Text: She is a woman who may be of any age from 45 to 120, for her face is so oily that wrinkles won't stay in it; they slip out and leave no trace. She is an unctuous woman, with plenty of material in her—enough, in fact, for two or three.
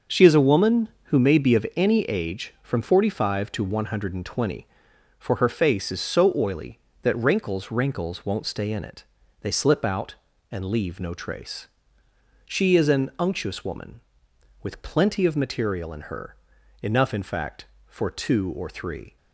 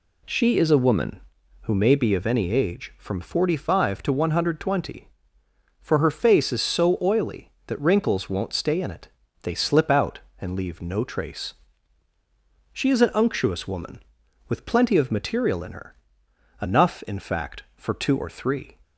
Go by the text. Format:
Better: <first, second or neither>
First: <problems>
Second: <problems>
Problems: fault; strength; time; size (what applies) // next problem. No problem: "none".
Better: second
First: starts louder than the rest; until 1.2 s; 6.5 dB // says "wrinkles" twice; at 7.7 s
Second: none